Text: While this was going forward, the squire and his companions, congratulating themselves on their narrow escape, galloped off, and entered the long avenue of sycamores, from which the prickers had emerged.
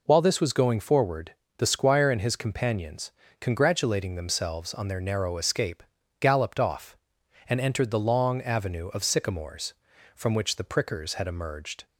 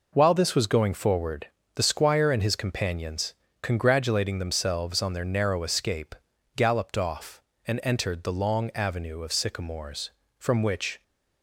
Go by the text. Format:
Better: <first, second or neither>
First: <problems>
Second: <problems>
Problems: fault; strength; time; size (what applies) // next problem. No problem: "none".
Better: first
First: none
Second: stops before "the prickers had emerged"; at 11.0 s